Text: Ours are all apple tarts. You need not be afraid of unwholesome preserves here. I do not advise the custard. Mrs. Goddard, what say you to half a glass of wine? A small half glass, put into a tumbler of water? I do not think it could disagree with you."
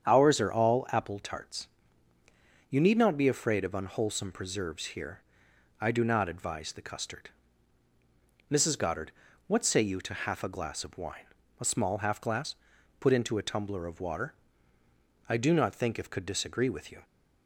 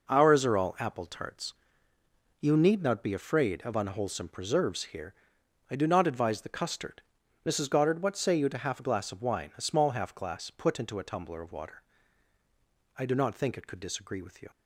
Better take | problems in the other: second | starts louder than the rest; strong; until 1.1 s; 8 dB // says "if" for "it"; at 15.9 s

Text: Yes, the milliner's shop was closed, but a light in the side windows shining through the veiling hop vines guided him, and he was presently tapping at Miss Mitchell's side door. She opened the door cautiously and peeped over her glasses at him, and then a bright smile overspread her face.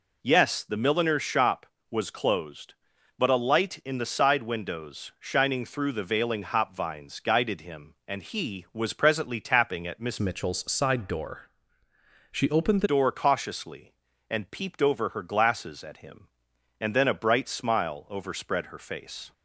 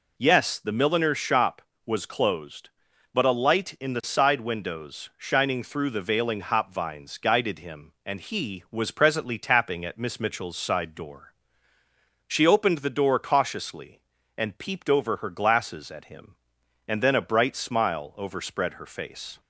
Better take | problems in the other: second | changes voice from "Mitchell's" to "the"; from 10.1 to 12.8 s; 2.7 s long

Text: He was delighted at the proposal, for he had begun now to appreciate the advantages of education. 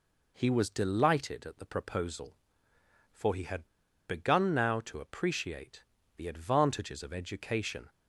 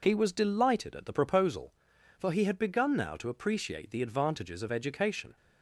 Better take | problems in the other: second | pauses between "had" and "begun"; at 3.6 s; 0.42 s long // pauses between "appreciate" and "the"; slight; at 5.8 s; 0.34 s long

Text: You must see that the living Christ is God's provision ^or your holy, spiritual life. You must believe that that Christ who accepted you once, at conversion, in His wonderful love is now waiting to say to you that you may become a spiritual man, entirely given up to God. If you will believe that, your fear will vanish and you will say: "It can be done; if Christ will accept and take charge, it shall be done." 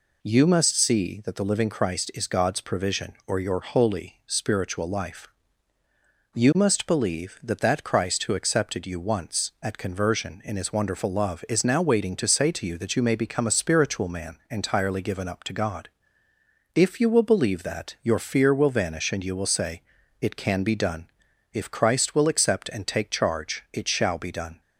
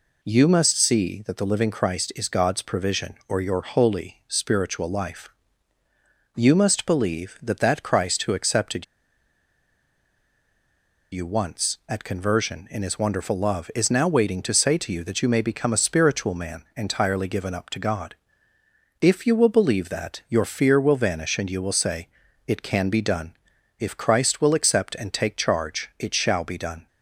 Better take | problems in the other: first | pauses between "accepted" and "you"; strong; at 8.8 s; 2.2 s long

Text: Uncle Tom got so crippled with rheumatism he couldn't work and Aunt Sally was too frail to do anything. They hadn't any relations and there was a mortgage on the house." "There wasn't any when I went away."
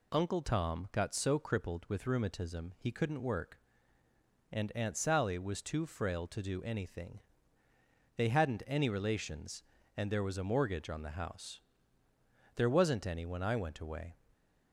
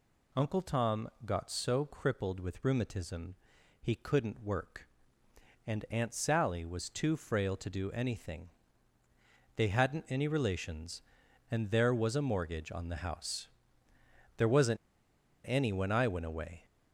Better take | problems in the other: first | pauses between "Tom" and "got"; slight; at 1.0 s; 0.18 s long // pauses between "rheumatism" and "he"; noticeable; at 3.3 s; 0.48 s long // pauses between "wasn't" and "any"; noticeable; at 14.7 s; 0.69 s long

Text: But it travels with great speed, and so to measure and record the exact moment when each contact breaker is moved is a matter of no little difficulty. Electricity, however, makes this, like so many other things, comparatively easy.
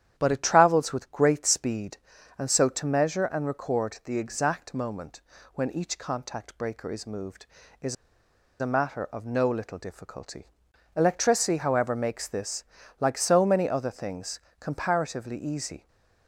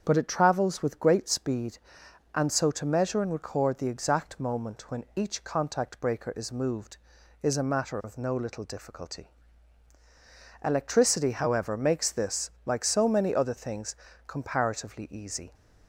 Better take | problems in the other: second | starts louder than the rest; strong; until 1.1 s; 10 dB; also in the second // pauses between "moment" and "when"; slight; at 5.2 s; 0.34 s long // pauses between "is" and "a"; noticeable; at 7.9 s; 0.66 s long

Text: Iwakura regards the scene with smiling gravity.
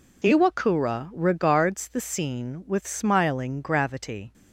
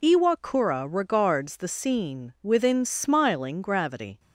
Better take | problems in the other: first | says "within" for "with"; at 2.4 s

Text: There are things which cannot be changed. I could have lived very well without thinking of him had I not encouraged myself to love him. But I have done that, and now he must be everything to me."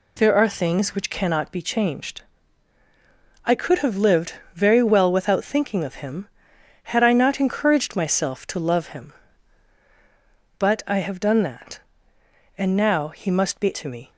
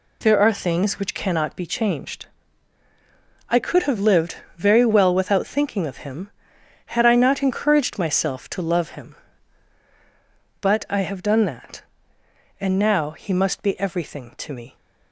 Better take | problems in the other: second | pauses between "lived" and "very"; slight; at 4.3 s; 0.22 s long; slight in the second // skips "everything"; at 13.7 s

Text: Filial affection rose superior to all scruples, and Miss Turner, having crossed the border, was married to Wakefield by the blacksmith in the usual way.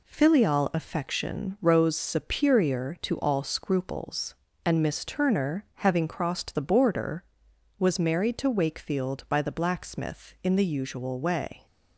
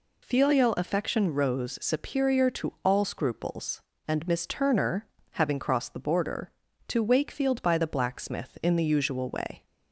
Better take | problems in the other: first | skips "was married"; at 6.6 s

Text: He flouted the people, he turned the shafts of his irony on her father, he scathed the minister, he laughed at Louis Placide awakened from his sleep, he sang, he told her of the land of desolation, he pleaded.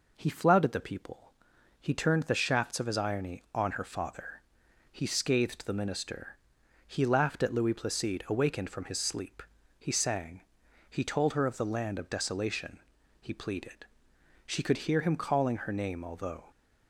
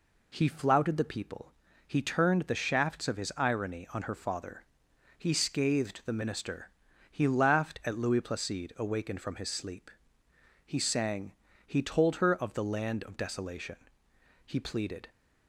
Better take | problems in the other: second | goes on to say "She could hear him calling her name although"; strong; from 14.4 s on; 2.0 s long

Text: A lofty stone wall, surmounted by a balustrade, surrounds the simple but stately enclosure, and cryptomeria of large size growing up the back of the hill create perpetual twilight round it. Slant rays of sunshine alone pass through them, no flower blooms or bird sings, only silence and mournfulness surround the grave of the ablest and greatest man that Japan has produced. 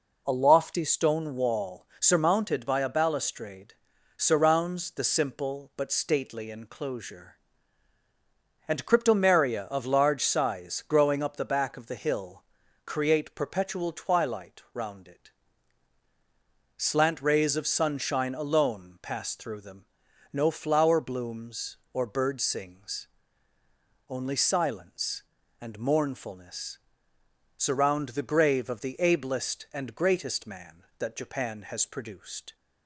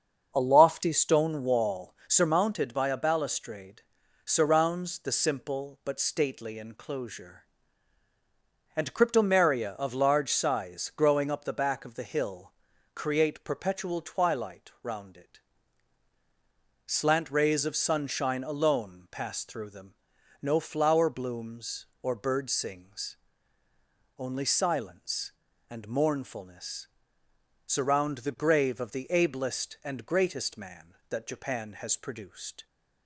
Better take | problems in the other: first | starts louder than the rest; until 2.1 s; 6.5 dB // pauses between "hill" and "create"; at 12.5 s; 0.42 s long; also in the first // pauses between "mournfulness" and "surround"; noticeable; at 26.8 s; 0.78 s long; noticeable in the first

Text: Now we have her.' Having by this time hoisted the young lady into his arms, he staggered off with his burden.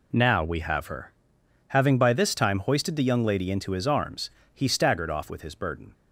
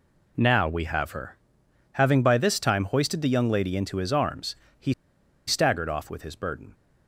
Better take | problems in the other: first | pauses between "he" and "staggered"; noticeable; at 4.9 s; 0.55 s long

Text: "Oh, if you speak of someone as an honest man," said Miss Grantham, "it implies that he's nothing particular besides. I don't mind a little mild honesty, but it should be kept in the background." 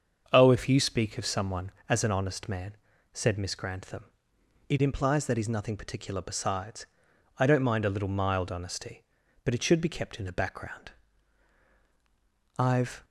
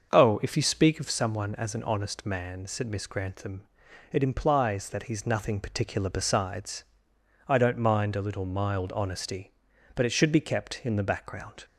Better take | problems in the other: second | starts louder than the rest; until 1.3 s; 7 dB; also in the second // goes on to say "I've"; slight; from 12.5 s on; 0.46 s long

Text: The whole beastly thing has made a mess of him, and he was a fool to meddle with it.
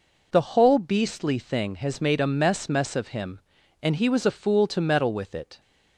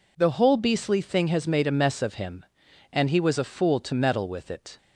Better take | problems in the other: second | says "mess" twice; at 2.6 s

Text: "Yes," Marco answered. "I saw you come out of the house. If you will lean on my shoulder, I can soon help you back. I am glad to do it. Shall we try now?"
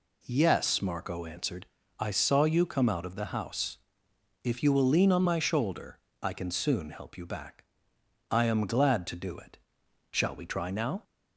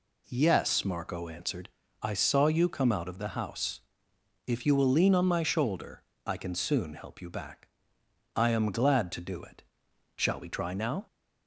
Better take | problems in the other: neither | none

